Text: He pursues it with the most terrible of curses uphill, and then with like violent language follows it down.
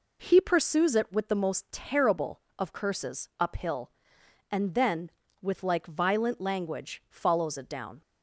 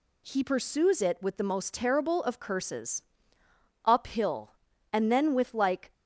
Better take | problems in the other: first | pauses between "curses" and "uphill"; noticeable; at 3.0 s; 0.80 s long // stops before "violent language follows it down"; at 5.9 s

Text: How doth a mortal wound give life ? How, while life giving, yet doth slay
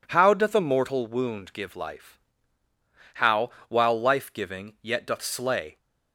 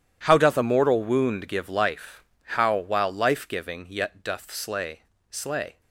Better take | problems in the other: first | says "slay" twice; at 5.3 s

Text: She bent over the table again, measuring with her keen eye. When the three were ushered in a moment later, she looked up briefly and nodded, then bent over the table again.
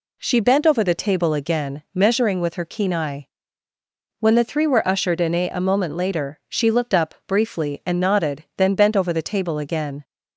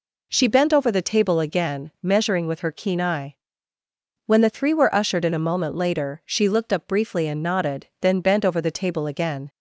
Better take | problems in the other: second | says "a" twice; at 5.5 s

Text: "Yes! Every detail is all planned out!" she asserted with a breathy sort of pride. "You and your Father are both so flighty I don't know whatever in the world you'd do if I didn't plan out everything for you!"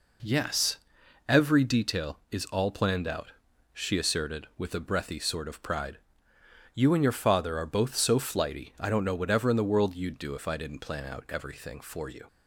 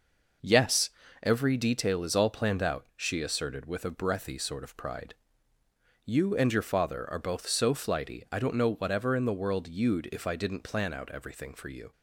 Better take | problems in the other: first | skips "do"; at 10.0 s

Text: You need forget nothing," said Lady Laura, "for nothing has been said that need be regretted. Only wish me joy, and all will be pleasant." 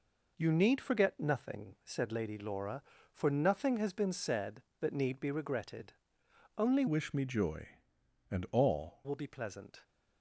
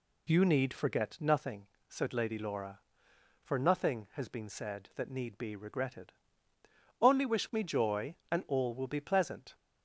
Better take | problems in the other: second | changes voice from "wish" to "all"; from 6.8 to 9.0 s; 2.2 s long

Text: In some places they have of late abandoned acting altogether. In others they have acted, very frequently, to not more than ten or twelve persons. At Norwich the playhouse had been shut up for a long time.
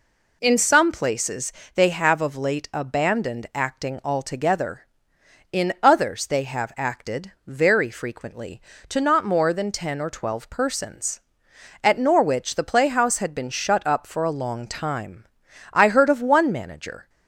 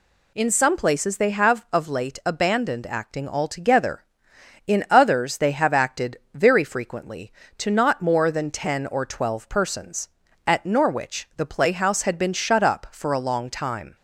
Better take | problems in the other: second | pauses between "places" and "they"; slight; at 1.5 s; 0.24 s long // goes on to say "I heard of one manager"; from 15.7 s on; 1.3 s long

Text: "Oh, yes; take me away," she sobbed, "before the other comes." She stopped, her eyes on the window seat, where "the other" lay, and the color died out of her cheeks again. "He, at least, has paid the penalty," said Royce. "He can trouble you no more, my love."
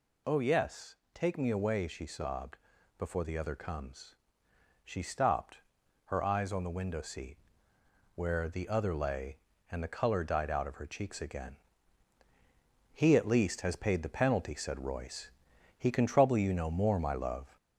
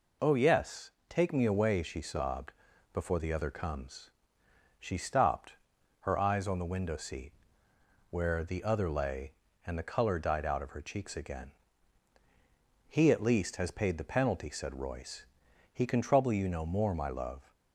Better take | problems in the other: second | gets louder; slight; throughout; 3 dB

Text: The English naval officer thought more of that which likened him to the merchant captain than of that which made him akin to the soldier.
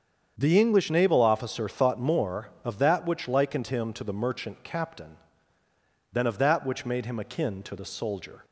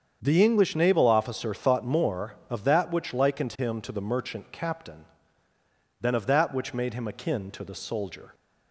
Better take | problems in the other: neither | starts louder than the rest; strong; the same in both

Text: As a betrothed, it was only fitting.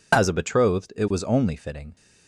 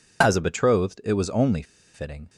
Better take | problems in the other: first | pauses between "only" and "fitting"; slight; at 1.6 s; 0.30 s long

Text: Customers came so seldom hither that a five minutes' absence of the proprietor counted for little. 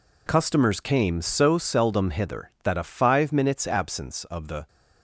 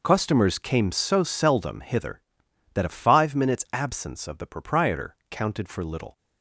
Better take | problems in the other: second | stops before "proprietor counted for little"; at 4.6 s

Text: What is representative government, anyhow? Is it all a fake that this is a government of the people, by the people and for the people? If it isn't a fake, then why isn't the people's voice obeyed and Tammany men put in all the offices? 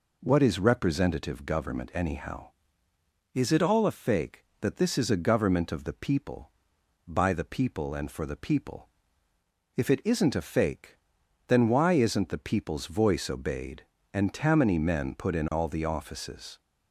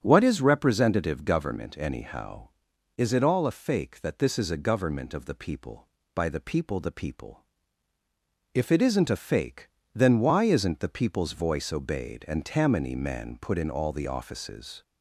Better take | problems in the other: first | starts louder than the rest; strong; until 1.0 s; 7.5 dB // skips "and for"; at 6.7 s

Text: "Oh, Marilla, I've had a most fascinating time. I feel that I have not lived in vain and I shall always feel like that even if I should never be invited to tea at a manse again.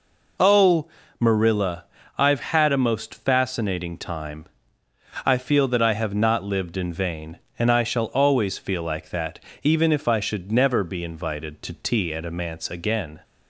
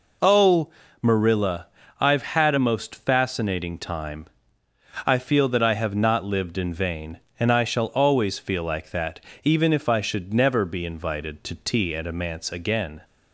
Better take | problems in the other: neither | pauses between "that" and "even"; slight; the same in both

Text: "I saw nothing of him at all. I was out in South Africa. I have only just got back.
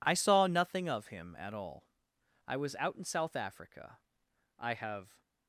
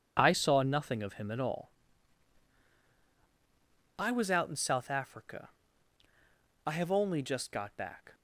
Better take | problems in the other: second | stops before "only just got back"; at 5.2 s

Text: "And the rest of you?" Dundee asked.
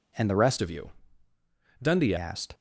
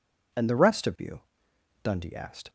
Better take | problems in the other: second | changes voice from "of" to "Dundee"; from 0.6 to 2.1 s; 1.5 s long

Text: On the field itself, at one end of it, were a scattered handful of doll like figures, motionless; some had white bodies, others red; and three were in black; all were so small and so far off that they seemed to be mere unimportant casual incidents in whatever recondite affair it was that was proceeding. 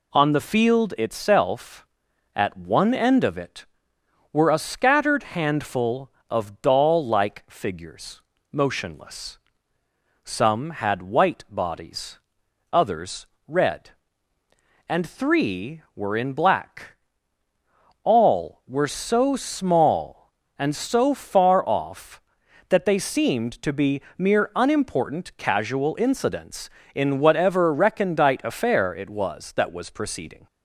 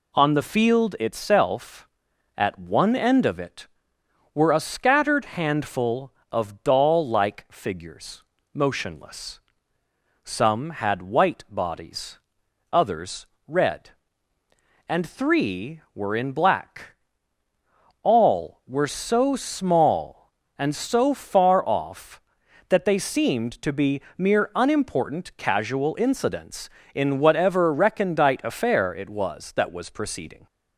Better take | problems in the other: neither | pauses between "others" and "red"; slight; the same in both // pauses between "be" and "mere"; slight; the same in both

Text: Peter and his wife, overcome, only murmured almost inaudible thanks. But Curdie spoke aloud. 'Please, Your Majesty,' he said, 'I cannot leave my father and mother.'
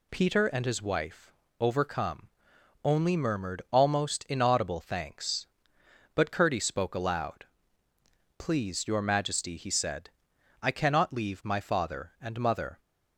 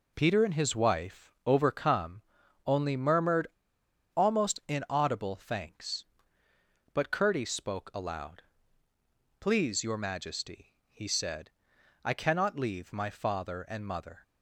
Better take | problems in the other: first | pauses between "murmured" and "almost"; noticeable; at 3.4 s; 0.66 s long

